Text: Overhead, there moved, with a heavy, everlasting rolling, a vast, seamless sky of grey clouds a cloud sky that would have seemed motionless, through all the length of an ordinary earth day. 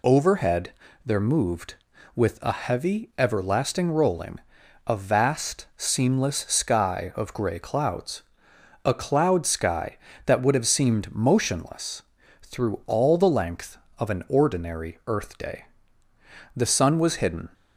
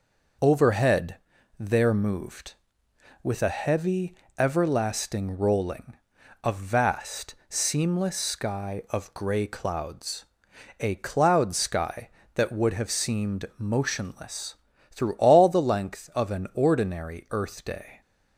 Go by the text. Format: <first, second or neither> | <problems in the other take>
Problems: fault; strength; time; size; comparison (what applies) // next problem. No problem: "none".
second | pauses between "clouds" and "a"; noticeable; at 8.2 s; 0.62 s long; noticeable in the second // goes on to say "The sun was hidden"; noticeable; from 16.5 s on; 0.94 s long